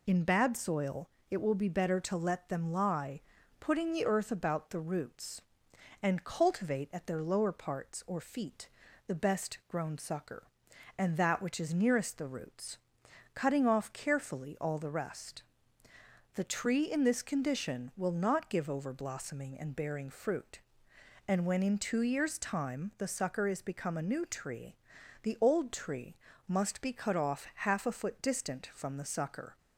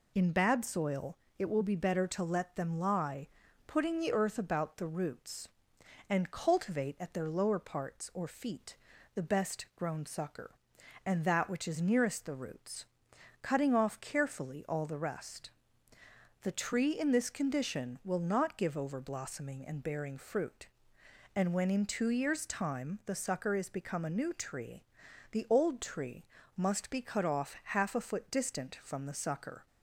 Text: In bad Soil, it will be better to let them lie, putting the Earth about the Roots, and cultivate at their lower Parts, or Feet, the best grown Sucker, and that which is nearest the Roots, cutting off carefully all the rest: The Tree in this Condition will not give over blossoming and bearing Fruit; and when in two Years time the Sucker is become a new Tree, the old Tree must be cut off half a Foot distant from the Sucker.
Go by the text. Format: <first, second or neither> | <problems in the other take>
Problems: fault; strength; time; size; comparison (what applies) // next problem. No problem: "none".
neither | pauses between "Tree" and "must"; slight; the same in both